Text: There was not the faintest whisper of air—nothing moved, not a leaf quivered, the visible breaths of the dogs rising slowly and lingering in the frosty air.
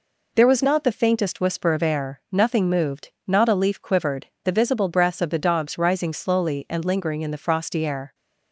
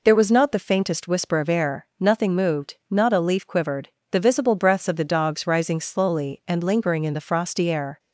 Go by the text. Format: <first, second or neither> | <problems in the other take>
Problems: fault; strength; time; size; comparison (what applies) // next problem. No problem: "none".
neither | none